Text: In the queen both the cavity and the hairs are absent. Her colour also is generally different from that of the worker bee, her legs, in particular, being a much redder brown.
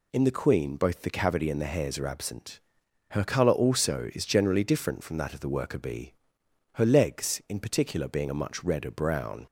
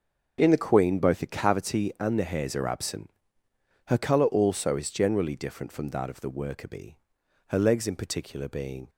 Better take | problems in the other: first | starts louder than the rest; until 1.4 s; 6.5 dB // stops before "a much redder brown"; at 8.8 s

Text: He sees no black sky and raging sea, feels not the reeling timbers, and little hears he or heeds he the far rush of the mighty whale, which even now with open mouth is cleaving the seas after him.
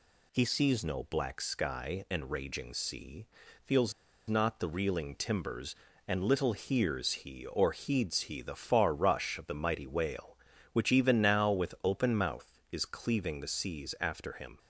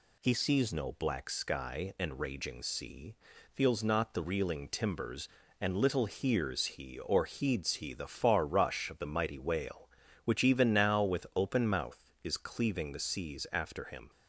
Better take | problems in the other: second | pauses between "feels" and "not"; at 3.9 s; 0.36 s long

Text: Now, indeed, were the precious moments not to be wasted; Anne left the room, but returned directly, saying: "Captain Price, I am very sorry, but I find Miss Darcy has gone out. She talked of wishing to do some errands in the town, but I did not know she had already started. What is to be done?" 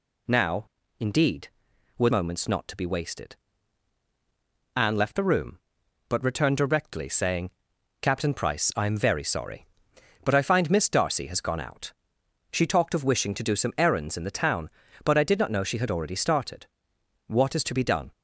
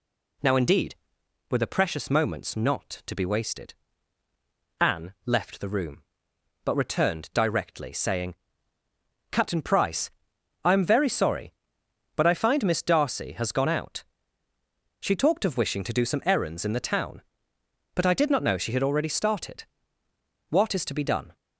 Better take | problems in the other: second | skips "the precious"; at 2.0 s

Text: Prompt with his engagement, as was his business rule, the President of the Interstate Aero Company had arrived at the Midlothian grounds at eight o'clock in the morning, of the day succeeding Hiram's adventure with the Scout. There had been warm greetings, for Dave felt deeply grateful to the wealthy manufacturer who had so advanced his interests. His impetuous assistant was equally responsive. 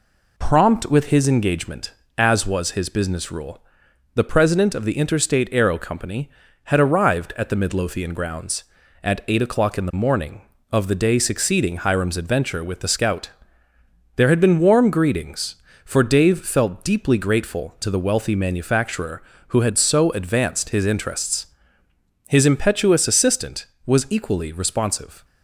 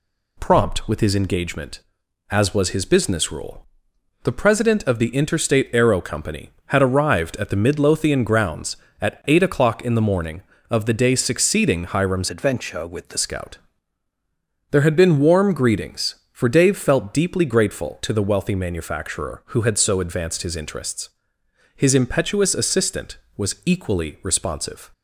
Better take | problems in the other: first | changes voice from "adventure" to "the"; from 12.3 to 13.1 s; 0.8 s long

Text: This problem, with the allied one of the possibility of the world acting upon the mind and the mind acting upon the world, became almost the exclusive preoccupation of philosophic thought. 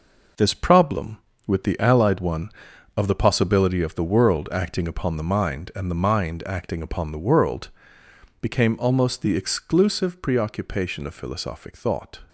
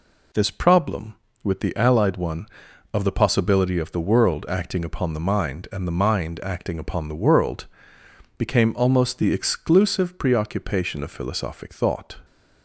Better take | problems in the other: second | gets quieter; strong; throughout; 7.5 dB

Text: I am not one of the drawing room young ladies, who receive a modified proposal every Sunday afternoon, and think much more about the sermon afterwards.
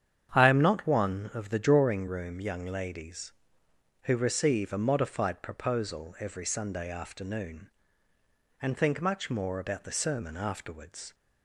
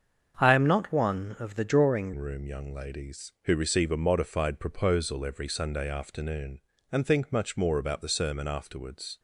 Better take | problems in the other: first | starts louder than the rest; strong; until 1.3 s; 7.5 dB; strong in the first // changes voice at "room"; from 2.1 s on; 7.0 s long

